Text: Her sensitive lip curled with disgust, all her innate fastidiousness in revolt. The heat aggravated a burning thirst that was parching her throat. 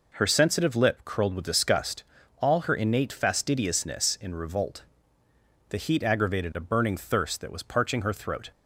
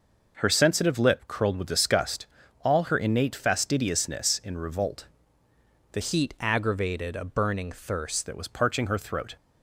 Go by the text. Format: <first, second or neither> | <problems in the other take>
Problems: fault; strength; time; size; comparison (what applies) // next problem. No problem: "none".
first | changes voice from "heat" to "thirst"; from 6.0 to 8.2 s; 2.2 s long